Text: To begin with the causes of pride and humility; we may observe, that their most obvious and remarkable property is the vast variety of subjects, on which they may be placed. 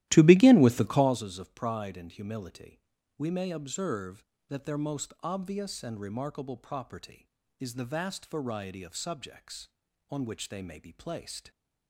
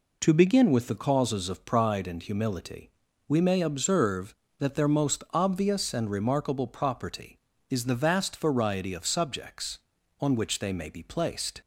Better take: second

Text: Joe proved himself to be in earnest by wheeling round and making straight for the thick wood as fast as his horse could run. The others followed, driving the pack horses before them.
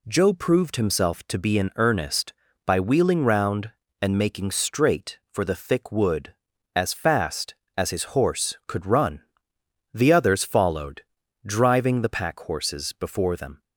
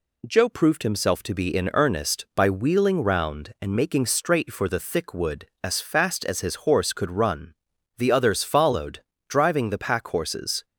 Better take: first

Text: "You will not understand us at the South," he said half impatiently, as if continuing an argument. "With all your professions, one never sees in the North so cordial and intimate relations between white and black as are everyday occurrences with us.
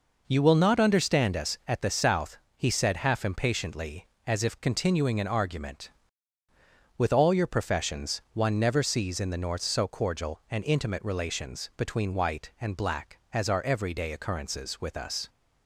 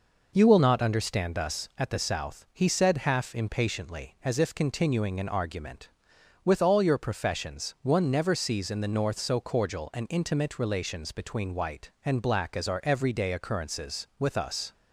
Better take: neither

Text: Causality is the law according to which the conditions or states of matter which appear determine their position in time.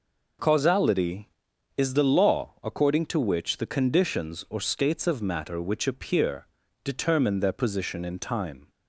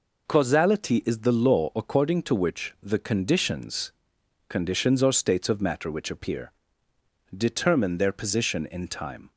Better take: first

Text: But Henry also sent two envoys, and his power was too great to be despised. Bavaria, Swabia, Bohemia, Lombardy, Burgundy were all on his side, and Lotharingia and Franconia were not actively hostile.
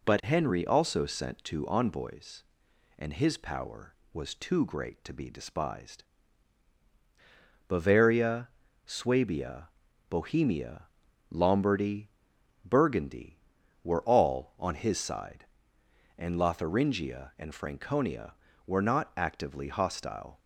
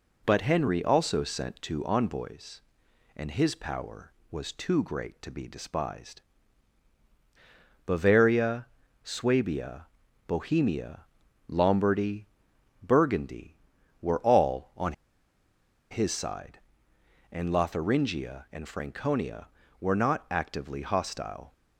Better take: first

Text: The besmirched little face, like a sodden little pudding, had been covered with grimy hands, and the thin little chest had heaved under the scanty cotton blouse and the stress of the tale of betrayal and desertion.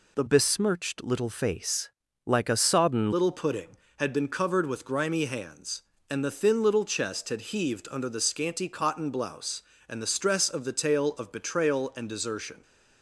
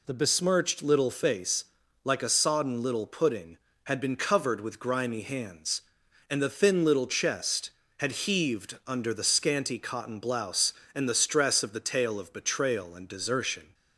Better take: second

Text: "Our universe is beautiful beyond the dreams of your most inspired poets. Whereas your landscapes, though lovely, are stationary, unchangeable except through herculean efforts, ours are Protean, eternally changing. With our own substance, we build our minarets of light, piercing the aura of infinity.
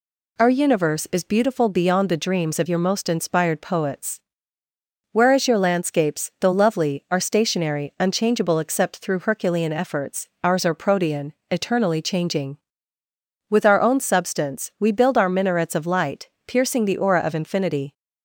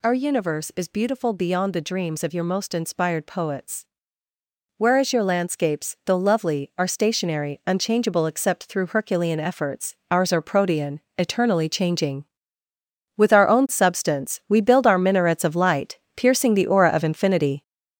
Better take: first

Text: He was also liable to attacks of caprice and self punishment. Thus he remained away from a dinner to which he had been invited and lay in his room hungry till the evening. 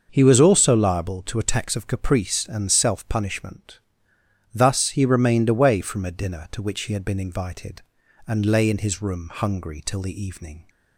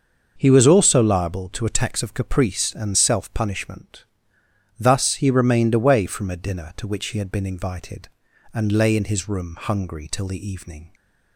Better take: neither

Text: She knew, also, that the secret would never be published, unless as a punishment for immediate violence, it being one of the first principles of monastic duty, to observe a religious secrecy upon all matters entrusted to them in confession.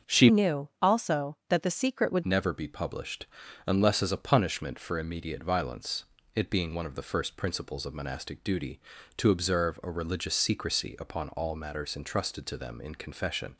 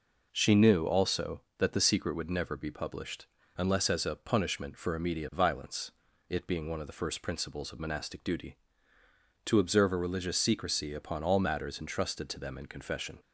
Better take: second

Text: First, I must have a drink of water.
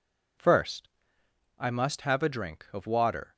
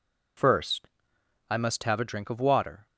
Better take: neither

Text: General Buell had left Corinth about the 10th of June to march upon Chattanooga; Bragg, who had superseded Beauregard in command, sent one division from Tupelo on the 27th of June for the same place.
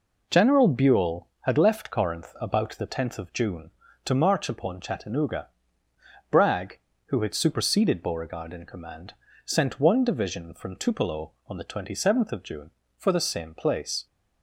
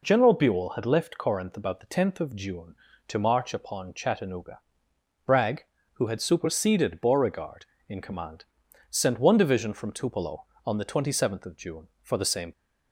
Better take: first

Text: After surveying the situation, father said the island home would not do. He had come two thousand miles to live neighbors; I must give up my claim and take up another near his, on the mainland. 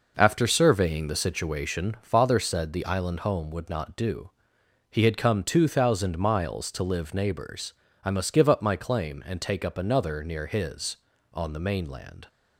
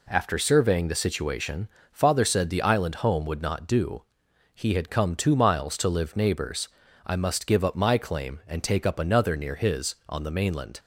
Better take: first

